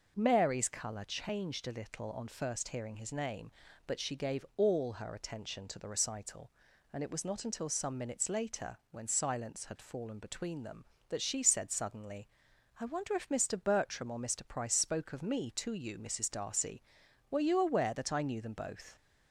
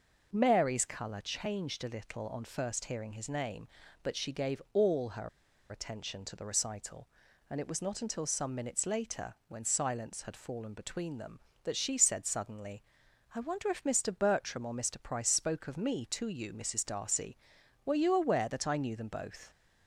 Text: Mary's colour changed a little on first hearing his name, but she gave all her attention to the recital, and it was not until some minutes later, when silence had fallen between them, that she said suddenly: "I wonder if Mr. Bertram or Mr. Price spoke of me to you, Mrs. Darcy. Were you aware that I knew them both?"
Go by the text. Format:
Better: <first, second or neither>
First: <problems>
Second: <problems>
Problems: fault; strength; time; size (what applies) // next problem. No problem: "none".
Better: first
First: none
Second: pauses between "her" and "attention"; at 5.2 s; 0.41 s long